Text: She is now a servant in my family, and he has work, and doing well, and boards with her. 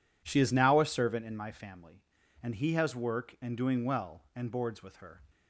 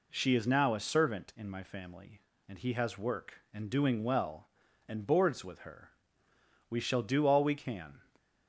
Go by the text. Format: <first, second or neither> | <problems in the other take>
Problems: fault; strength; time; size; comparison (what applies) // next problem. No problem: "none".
first | goes on to say "We shall do all we can"; from 6.6 s on; 1.3 s long